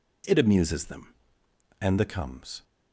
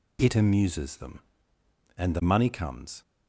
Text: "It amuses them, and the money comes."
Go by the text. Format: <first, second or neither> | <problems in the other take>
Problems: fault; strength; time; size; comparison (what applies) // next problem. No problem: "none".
second | skips "money"; at 2.0 s